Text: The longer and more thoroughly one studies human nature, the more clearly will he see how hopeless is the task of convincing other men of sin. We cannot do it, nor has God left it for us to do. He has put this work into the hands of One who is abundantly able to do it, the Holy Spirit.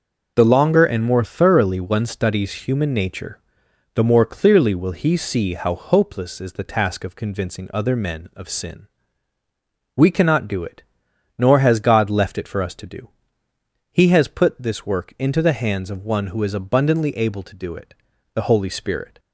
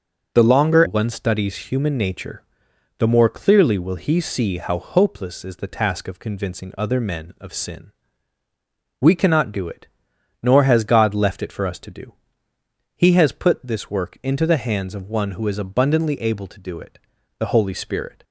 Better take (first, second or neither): first